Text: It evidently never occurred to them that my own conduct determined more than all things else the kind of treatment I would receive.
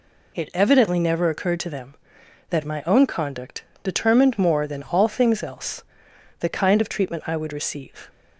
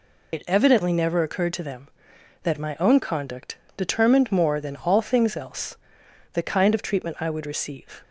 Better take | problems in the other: first | loses the start of "It"; at 0.3 s; 40 ms // pauses between "conduct" and "determined"; slight; at 3.5 s; 0.22 s long; slight in the first // pauses between "else" and "the"; noticeable; at 5.7 s; 0.56 s long; noticeable in the first

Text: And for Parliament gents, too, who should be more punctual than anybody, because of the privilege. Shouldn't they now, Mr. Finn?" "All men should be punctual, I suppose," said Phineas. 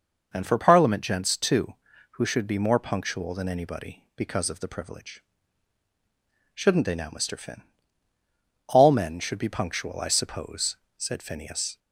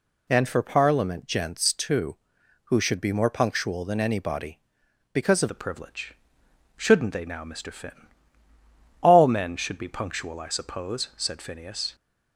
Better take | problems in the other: first | changes voice at "the"; from 5.4 s on; 6.5 s long

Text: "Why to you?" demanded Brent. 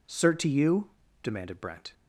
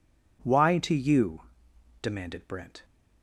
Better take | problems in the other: second | says "Cert" for "Why"; at 0.0 s

